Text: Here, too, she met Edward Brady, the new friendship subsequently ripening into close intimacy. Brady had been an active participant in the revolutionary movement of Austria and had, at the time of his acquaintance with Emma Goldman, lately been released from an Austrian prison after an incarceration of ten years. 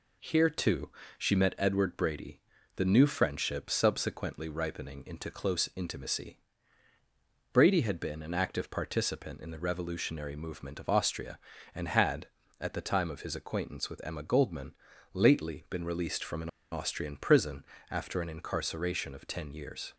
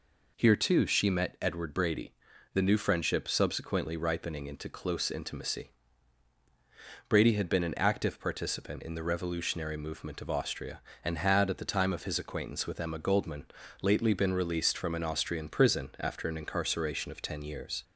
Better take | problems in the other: second | pauses between "an" and "Austrian"; slight; at 16.4 s; 0.22 s long // pauses between "prison" and "after"; slight; at 17.6 s; 0.24 s long

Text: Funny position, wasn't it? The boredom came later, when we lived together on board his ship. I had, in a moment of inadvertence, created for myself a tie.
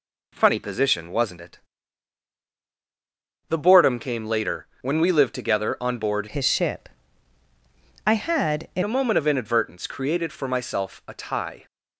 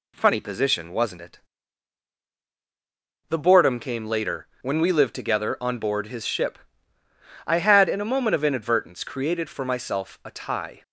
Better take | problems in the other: second | changes voice from "his" to "in"; from 6.2 to 8.8 s; 2.6 s long

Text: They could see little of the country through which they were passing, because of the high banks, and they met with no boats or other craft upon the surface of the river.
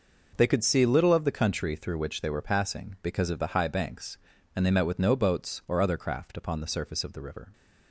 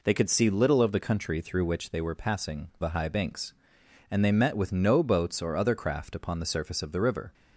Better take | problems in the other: first | skips "because of"; at 2.7 s

